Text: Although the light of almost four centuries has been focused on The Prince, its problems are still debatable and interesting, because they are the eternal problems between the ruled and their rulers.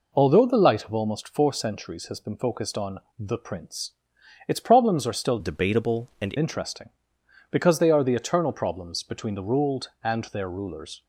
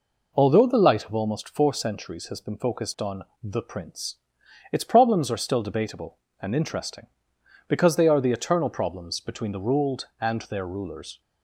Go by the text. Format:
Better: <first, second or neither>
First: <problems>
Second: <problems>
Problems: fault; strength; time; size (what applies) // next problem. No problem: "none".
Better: second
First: pauses between "on" and "The"; slight; at 3.0 s; 0.18 s long // changes voice from "debatable" to "and"; from 5.3 to 6.3 s; 1.0 s long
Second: pauses between "on" and "The"; slight; at 3.2 s; 0.18 s long